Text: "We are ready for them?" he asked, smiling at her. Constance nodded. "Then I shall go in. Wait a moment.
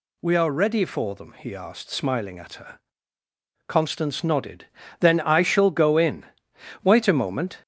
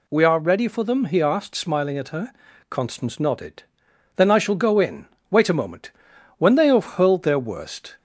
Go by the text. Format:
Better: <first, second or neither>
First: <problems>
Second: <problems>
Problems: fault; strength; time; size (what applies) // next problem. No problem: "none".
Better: first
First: none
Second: goes on to say "When they have hurled their worst"; from 6.3 s on; 1.6 s long